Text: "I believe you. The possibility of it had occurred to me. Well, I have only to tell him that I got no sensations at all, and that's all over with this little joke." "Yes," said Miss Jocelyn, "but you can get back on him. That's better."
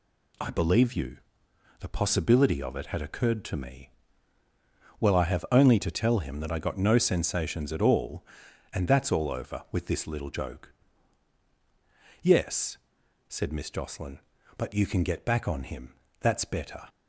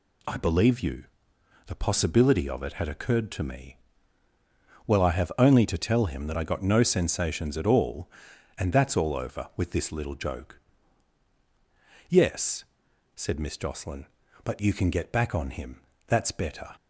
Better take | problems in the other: neither | none

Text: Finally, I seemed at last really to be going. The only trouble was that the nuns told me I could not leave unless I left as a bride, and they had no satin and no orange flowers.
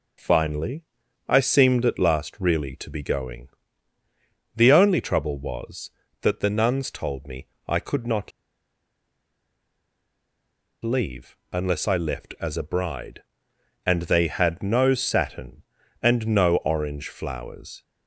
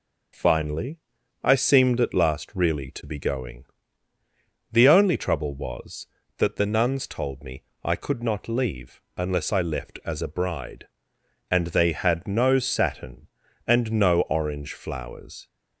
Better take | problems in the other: second | starts louder than the rest; noticeable; until 1.6 s; 6 dB // pauses between "me" and "I"; slight; at 7.4 s; 0.22 s long; slight in the second // pauses between "not" and "leave"; strong; at 8.3 s; 2.5 s long // pauses between "leave" and "unless"; slight; at 11.3 s; 0.16 s long; slight in the second

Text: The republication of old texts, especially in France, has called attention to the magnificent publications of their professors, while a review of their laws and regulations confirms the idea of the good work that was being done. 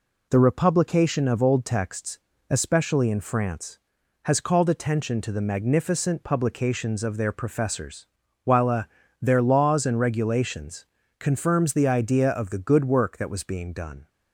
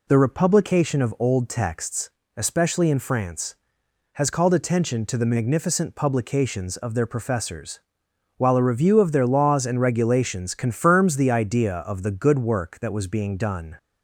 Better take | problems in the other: second | skips "review of"; at 9.0 s // pauses between "regulations" and "confirms"; slight; at 10.8 s; 0.34 s long

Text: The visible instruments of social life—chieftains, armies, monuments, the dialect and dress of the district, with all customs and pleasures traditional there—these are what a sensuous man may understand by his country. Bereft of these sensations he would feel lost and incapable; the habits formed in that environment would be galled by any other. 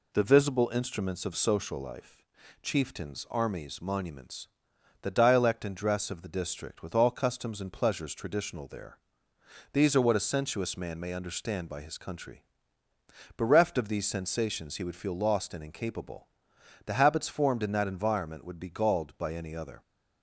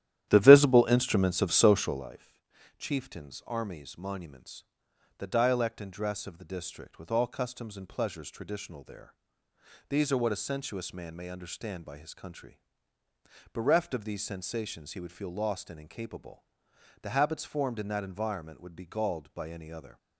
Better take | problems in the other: first | starts louder than the rest; strong; until 2.1 s; 12 dB

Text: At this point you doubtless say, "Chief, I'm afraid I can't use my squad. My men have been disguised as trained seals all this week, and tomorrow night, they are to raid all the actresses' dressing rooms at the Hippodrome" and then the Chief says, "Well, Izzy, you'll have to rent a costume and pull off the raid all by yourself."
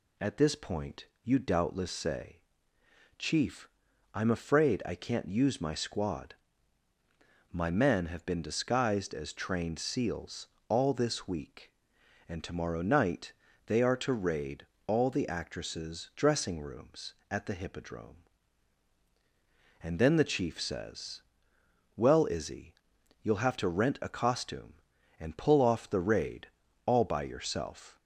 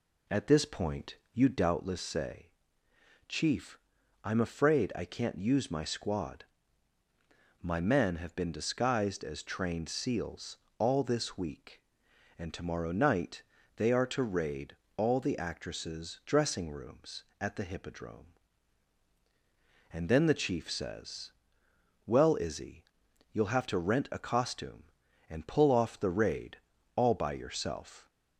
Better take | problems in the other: first | starts louder than the rest; slight; until 1.7 s; 2.5 dB // pauses between "point" and "you"; slight; at 1.1 s; 0.18 s long; slight in the first // pauses between "seals" and "all"; slight; at 10.5 s; 0.22 s long; slight in the first // pauses between "raid" and "all"; slight; at 14.7 s; 0.22 s long; slight in the first // pauses between "raid" and "all"; at 26.5 s; 0.38 s long; also in the first

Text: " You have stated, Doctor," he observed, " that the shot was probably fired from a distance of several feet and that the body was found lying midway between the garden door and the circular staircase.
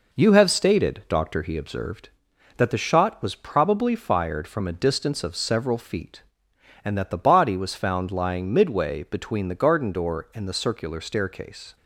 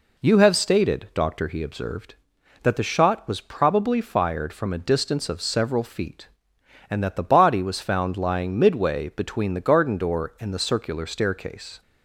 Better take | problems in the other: second | gets quieter; slight; throughout; 2 dB

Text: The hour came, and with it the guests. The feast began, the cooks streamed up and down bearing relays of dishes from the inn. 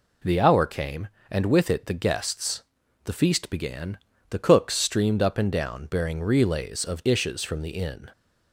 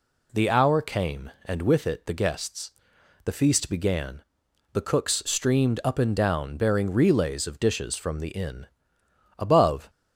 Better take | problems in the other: first | goes on to say "Above"; from 9.3 s on; 0.50 s long

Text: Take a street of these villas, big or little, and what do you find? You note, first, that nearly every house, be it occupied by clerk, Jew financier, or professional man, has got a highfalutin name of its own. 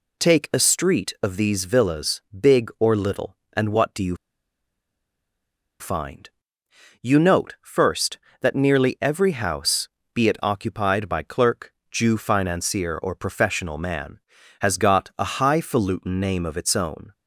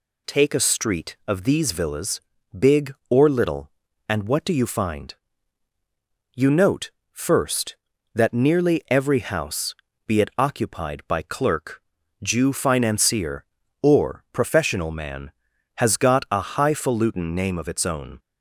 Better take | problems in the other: second | pauses between "you" and "find"; strong; at 4.1 s; 1.6 s long

